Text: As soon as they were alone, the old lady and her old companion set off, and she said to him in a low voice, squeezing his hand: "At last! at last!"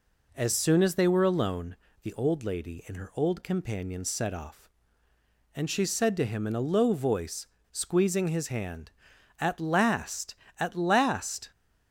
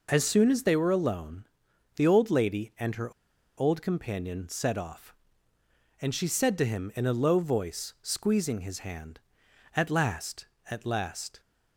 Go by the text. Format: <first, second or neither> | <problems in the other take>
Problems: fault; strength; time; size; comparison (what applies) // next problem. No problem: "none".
first | pauses between "her" and "old"; noticeable; at 3.1 s; 0.46 s long